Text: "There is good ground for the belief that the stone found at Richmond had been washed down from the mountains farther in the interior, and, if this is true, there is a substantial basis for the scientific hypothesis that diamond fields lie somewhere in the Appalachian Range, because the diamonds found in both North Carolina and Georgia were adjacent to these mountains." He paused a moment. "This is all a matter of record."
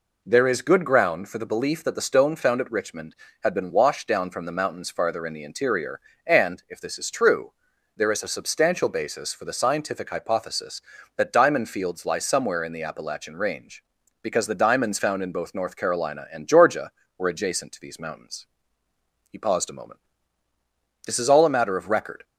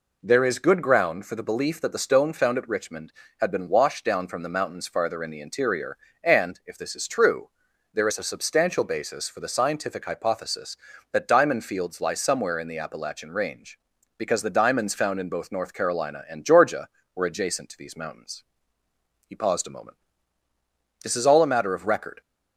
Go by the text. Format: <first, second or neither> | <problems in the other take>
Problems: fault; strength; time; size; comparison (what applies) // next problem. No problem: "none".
neither | none